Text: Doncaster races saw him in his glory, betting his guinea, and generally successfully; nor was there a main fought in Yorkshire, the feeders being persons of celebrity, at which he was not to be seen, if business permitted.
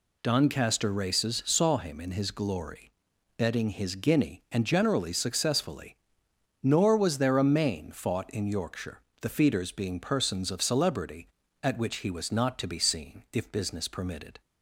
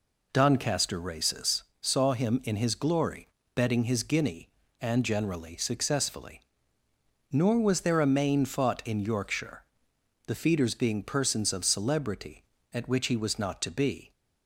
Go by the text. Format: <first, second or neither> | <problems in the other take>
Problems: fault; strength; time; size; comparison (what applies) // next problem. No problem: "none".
first | pauses between "races" and "saw"; slight; at 1.6 s; 0.18 s long // stops before "seen if business permitted"; at 14.1 s